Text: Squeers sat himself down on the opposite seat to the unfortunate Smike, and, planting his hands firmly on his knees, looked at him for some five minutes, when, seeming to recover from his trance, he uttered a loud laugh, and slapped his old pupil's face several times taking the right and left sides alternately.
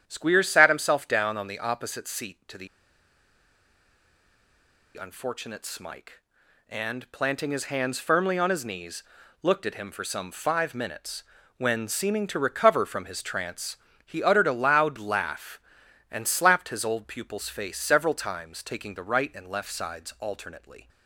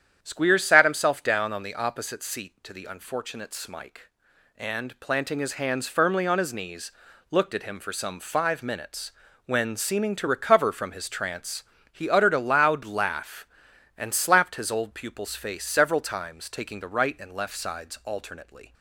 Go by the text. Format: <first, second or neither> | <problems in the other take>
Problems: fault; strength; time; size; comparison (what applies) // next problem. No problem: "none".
second | starts louder than the rest; strong; until 1.0 s; 9 dB; strong in the second // pauses between "the" and "unfortunate"; strong; at 2.6 s; 2.2 s long